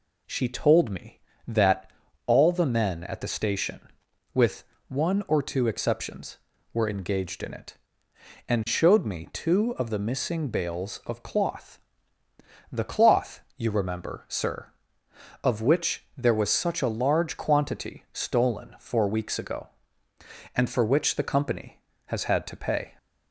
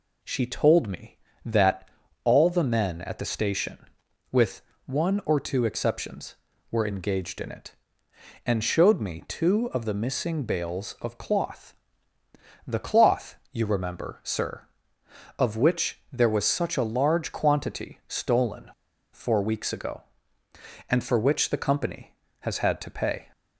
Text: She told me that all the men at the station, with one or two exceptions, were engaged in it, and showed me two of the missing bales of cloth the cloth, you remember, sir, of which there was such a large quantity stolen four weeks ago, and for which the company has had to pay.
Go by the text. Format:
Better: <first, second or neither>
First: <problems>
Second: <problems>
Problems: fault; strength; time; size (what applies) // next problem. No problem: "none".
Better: first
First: pauses between "that" and "all"; slight; at 1.9 s; 0.36 s long // pauses between "with" and "one"; slight; at 4.6 s; 0.24 s long // pauses between "cloth" and "the"; noticeable; at 11.7 s; 0.90 s long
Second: pauses between "that" and "all"; slight; at 1.8 s; 0.36 s long // pauses between "with" and "one"; slight; at 4.6 s; 0.24 s long // pauses between "cloth" and "the"; noticeable; at 11.7 s; 0.90 s long // pauses between "stolen" and "four"; at 18.7 s; 0.42 s long